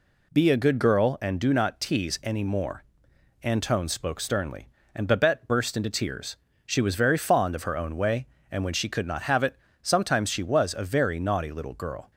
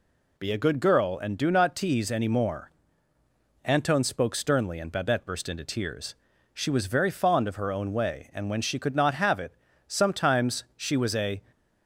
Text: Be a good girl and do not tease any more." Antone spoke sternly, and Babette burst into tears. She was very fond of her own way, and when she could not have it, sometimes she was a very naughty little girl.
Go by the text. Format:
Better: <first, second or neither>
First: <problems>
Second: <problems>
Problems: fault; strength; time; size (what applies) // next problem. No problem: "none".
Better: first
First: none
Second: stops before "very naughty little girl"; at 11.5 s